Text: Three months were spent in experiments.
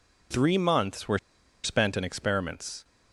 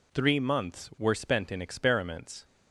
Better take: second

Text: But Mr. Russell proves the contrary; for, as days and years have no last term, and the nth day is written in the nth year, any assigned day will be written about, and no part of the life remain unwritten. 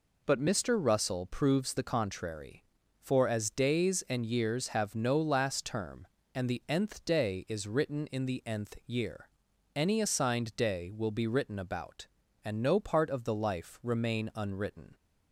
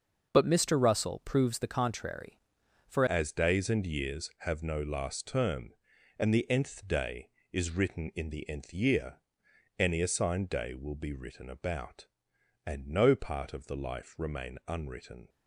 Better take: first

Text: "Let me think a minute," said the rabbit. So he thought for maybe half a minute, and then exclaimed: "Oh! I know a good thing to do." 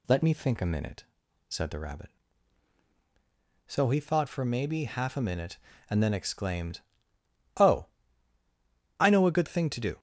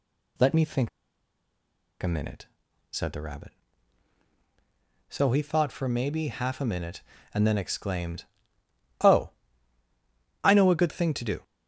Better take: first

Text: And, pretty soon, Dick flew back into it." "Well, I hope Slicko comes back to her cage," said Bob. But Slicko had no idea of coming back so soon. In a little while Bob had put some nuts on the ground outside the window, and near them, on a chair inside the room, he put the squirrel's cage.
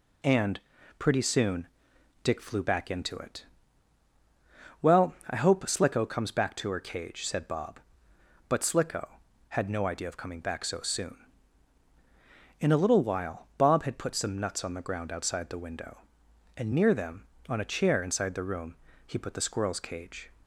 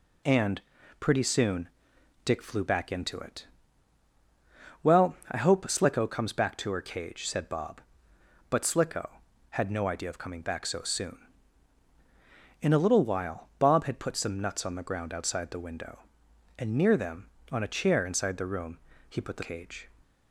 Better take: first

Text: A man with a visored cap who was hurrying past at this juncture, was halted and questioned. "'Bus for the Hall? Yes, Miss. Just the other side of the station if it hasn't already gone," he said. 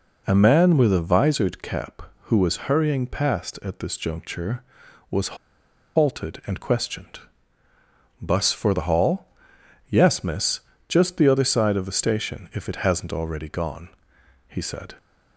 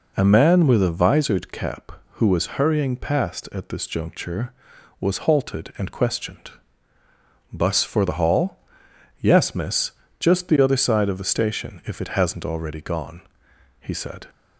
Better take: second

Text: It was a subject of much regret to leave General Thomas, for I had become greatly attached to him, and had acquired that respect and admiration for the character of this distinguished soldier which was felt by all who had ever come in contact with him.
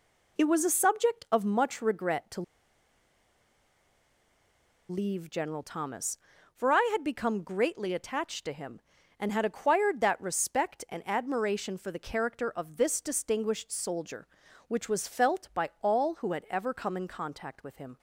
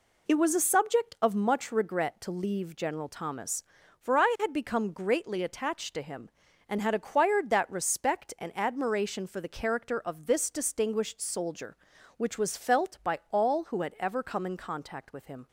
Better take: second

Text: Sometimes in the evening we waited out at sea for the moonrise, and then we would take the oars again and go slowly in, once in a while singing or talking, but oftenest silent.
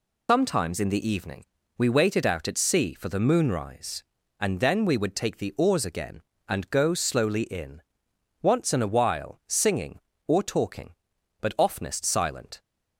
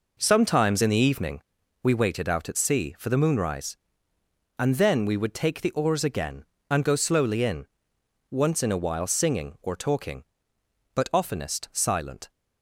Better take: second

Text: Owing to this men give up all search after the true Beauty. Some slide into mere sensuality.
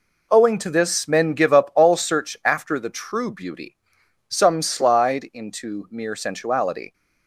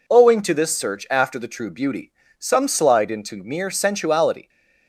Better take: first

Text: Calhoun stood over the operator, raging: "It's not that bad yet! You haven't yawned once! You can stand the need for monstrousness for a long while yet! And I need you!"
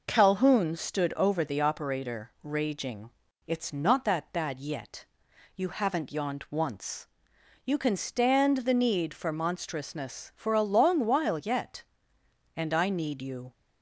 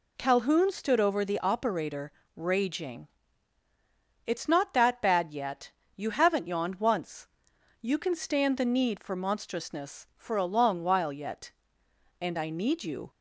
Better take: neither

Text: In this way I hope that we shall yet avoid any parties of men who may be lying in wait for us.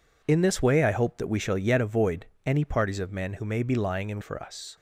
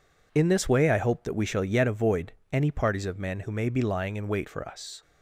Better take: second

